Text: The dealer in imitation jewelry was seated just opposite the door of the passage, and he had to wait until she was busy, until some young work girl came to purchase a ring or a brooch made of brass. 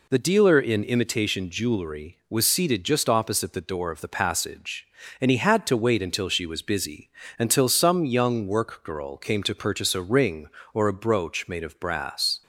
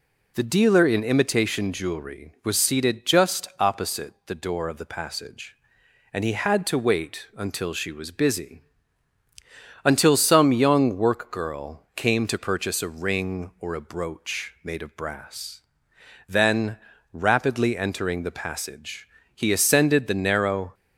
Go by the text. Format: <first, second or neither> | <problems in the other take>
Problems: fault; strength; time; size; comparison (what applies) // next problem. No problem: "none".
first | goes on to say "Then rapidly entering the passage he ascended the narrow"; strong; from 16.2 s on; 4.4 s long